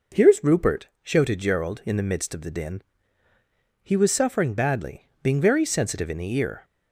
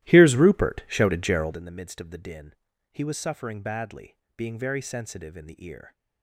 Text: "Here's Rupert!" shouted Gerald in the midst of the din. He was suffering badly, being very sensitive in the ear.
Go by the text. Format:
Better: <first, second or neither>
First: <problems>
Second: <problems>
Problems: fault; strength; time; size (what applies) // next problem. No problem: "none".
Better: first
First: none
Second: starts louder than the rest; strong; until 1.7 s; 15 dB